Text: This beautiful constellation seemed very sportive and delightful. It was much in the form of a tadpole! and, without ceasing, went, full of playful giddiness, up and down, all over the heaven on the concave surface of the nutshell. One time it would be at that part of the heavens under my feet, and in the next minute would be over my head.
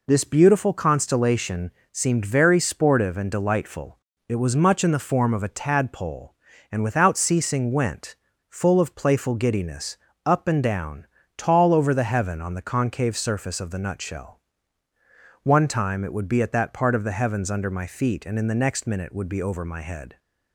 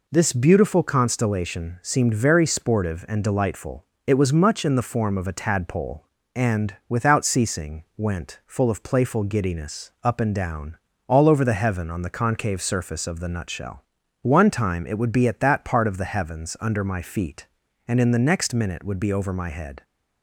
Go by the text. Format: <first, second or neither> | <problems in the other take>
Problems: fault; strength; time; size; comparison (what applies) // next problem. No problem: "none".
second | pauses between "constellation" and "seemed"; slight; at 1.7 s; 0.20 s long // says "tall" for "all"; at 11.3 s